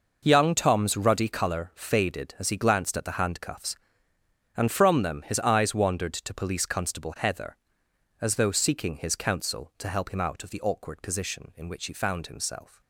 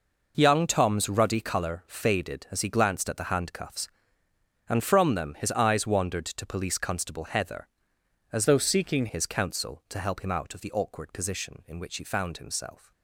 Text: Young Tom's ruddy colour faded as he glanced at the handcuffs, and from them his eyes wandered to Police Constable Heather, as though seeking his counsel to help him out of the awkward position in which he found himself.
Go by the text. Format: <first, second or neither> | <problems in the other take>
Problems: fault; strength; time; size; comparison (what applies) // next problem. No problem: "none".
first | changes voice from "though" to "seeking"; from 8.4 to 9.0 s; 0.6 s long